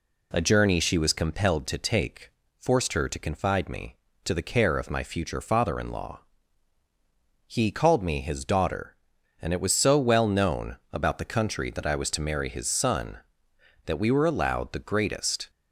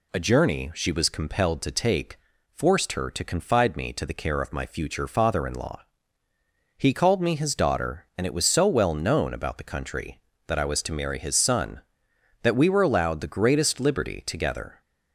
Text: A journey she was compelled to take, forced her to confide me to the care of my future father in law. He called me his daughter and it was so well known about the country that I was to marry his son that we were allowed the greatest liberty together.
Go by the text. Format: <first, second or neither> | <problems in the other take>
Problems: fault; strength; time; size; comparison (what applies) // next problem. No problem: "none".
second | stops before "liberty together"; at 15.4 s